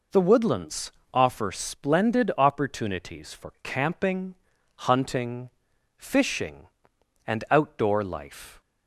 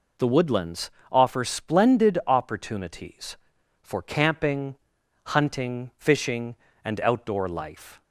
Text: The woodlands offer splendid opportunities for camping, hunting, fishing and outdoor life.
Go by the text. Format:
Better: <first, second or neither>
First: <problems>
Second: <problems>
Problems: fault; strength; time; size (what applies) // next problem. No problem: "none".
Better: neither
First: pauses between "woodlands" and "offer"; slight; at 0.9 s; 0.24 s long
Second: pauses between "woodlands" and "offer"; slight; at 0.9 s; 0.20 s long